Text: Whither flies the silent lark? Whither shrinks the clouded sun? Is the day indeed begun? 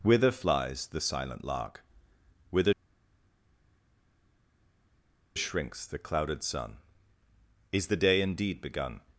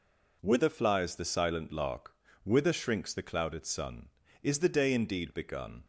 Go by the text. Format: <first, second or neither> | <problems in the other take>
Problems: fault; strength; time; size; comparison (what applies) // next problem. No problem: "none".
second | pauses between "Whither" and "shrinks"; strong; at 2.7 s; 2.6 s long